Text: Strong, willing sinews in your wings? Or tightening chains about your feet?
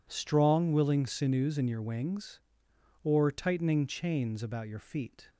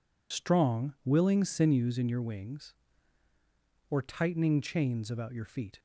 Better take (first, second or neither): first